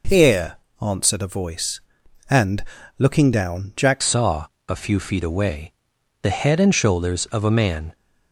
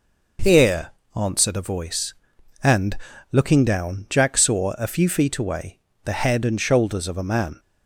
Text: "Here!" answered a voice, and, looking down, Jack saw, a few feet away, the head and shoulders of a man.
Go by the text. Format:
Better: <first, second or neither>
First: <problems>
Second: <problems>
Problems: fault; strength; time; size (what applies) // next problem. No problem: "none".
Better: second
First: changes voice at "saw"; from 4.0 s on; 3.9 s long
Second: none